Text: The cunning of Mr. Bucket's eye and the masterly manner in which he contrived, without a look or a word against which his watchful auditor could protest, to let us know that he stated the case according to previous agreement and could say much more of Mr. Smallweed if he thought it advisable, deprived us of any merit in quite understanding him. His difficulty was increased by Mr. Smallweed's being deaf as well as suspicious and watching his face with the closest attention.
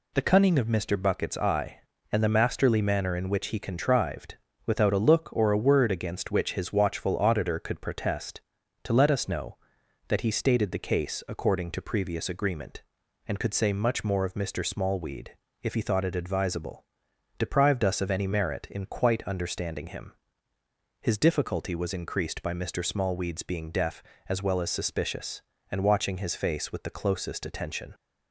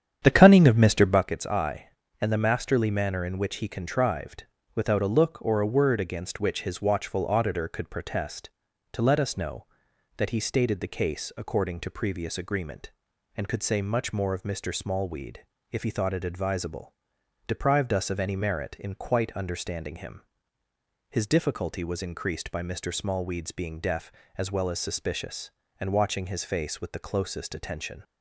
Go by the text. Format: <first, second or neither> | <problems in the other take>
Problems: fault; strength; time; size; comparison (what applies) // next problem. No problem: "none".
first | starts louder than the rest; strong; until 1.3 s; 9 dB // pauses between "Smallweed" and "if"; slight; at 15.3 s; 0.32 s long; slight in the first